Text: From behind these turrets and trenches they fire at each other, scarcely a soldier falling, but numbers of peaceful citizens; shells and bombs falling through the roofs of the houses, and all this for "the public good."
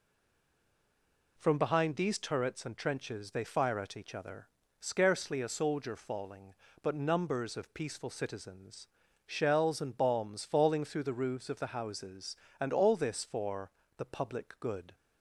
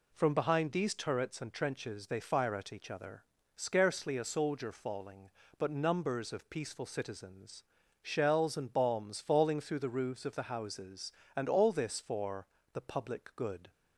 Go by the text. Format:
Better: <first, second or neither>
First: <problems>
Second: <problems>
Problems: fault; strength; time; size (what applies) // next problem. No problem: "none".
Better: second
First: stays silent before the first word; noticeable; until 1.3 s; 1.3 s long // pauses between "for" and "the"; slight; at 13.6 s; 0.28 s long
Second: pauses between "for" and "the"; slight; at 12.4 s; 0.28 s long